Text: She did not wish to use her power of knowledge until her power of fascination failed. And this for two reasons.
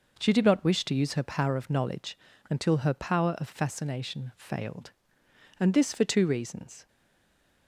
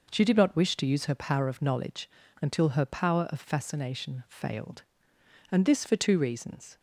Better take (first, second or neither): second